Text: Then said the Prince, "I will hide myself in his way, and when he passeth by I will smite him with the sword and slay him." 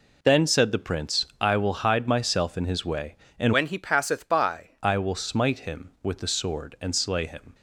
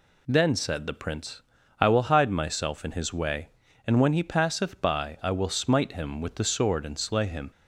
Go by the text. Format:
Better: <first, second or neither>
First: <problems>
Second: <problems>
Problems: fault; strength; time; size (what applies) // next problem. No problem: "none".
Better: second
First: changes voice from "when" to "by"; from 3.5 to 4.6 s; 1.1 s long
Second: none